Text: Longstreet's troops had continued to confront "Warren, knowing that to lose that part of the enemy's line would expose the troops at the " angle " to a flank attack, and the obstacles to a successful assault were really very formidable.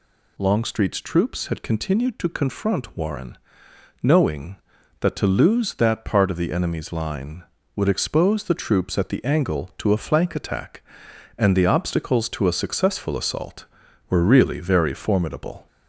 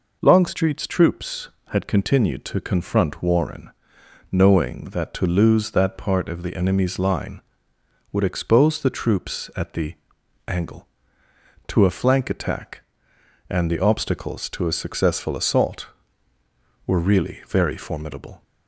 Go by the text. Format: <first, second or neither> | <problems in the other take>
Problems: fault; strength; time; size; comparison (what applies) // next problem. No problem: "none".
second | gets louder; slight; throughout; 2.5 dB